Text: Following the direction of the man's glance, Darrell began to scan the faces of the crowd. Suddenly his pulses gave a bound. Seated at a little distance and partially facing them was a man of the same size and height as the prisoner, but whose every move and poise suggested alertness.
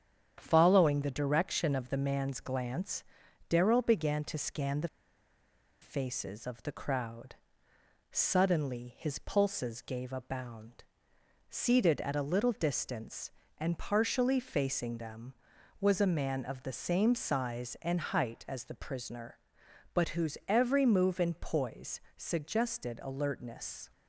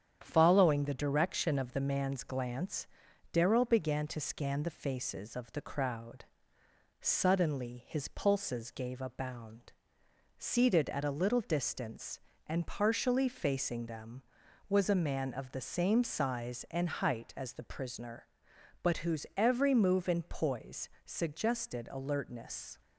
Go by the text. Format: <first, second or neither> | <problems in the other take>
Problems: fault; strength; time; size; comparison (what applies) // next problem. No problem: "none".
second | starts louder than the rest; strong; until 1.4 s; 8.5 dB; strong in the second // pauses between "the" and "faces"; noticeable; at 4.8 s; 0.94 s long // pauses between "poise" and "suggested"; slight; at 21.9 s; 0.16 s long; slight in the second